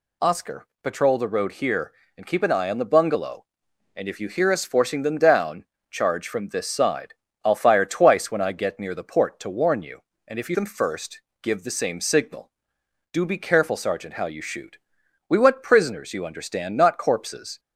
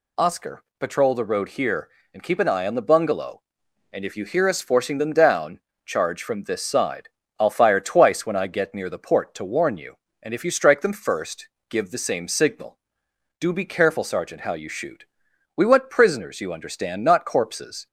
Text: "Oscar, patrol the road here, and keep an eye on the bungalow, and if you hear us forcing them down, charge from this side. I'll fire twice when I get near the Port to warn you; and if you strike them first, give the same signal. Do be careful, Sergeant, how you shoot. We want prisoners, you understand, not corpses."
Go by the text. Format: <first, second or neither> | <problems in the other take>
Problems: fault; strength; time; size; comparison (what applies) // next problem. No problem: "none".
second | skips "strike"; at 10.5 s